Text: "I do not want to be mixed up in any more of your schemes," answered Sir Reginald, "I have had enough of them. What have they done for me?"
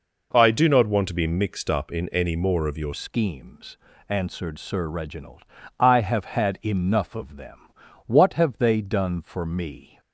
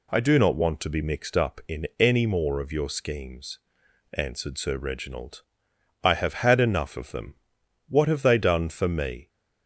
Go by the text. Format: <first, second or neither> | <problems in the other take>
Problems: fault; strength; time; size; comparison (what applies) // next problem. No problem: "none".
second | changes voice at "schemes"; from 2.9 s on; 7.0 s long